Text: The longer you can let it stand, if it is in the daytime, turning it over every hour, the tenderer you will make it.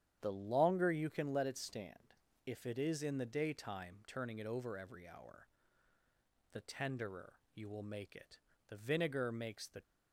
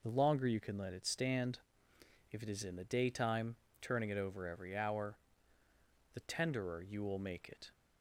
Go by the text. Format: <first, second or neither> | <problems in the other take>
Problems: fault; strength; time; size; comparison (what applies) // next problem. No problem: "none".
second | starts louder than the rest; strong; until 1.2 s; 9.5 dB // pauses between "tenderer" and "you"; slight; at 7.3 s; 0.16 s long // goes on to say "The vinegar makes the"; noticeable; from 8.6 s on; 1.1 s long